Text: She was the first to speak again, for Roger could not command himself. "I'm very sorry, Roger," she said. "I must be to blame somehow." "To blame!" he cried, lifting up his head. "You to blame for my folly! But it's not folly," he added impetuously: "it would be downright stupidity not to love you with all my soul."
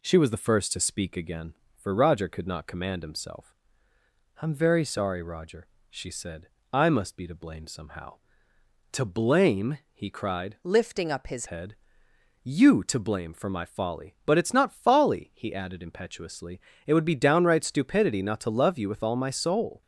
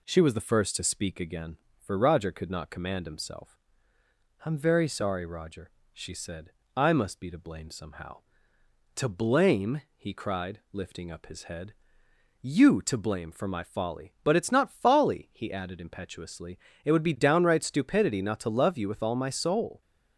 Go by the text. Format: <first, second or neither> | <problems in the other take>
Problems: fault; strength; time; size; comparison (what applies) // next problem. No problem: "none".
second | changes voice from "lifting" to "his"; from 10.6 to 11.4 s; 0.8 s long